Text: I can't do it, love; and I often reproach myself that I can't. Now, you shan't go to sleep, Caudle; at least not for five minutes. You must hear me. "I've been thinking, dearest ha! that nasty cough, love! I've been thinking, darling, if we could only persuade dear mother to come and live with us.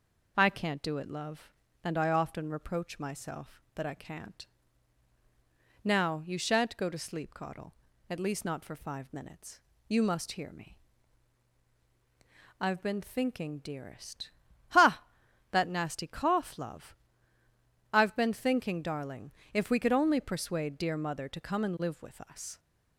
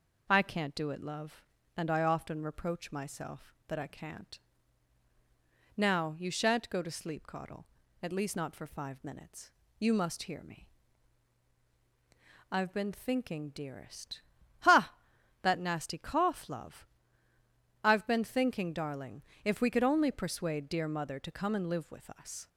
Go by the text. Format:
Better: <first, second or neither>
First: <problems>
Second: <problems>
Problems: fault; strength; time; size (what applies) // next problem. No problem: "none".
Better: neither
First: pauses between "dearest" and "ha"; at 14.3 s; 0.38 s long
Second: pauses between "dearest" and "ha"; at 14.2 s; 0.38 s long